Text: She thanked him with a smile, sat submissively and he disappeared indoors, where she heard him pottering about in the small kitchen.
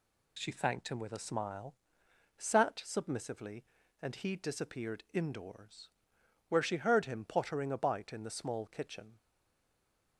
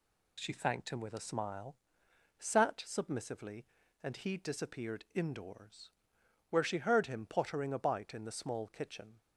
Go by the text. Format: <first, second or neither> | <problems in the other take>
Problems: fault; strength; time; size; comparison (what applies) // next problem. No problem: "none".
second | stays silent after the last word; from 9.1 s on; 1.0 s long